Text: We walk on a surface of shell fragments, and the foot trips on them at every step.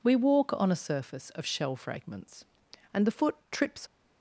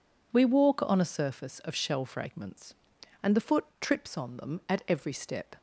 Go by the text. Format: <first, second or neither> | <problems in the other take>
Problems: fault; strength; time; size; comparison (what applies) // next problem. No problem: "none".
second | pauses between "foot" and "trips"; slight; at 3.3 s; 0.16 s long; slight in the second // stops before "on them at every step"; at 3.8 s